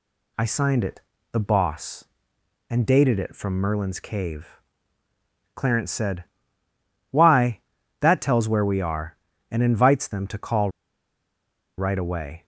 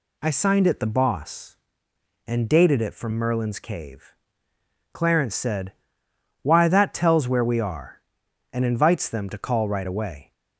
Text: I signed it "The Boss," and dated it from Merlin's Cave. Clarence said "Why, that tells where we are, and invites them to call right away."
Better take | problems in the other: second | pauses between "it" and "The"; slight; at 1.0 s; 0.30 s long // pauses between "said" and "Why"; noticeable; at 6.2 s; 0.88 s long; noticeable in the second // pauses between "call" and "right"; at 10.7 s; 1.0 s long

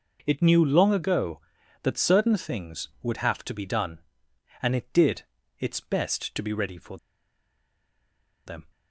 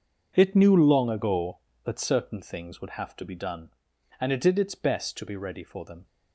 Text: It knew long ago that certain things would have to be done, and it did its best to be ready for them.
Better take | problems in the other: second | pauses between "did" and "its"; slight; at 5.2 s; 0.36 s long // pauses between "for" and "them"; strong; at 6.9 s; 1.4 s long

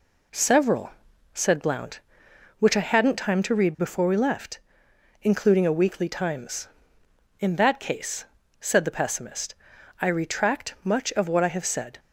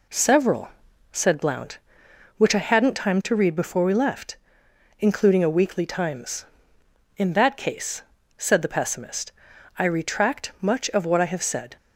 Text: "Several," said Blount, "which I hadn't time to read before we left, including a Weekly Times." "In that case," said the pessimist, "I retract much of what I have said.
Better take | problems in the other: neither | none

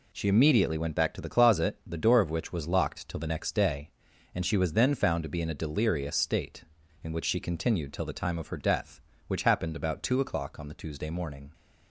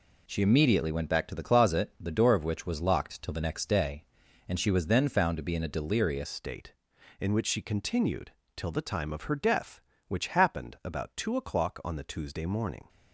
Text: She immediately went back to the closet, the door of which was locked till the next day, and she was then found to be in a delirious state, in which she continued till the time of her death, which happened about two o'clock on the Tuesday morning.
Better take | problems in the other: first | changes voice at "state"; from 6.2 s on; 6.6 s long // pauses between "continued" and "till"; slight; at 8.2 s; 0.26 s long

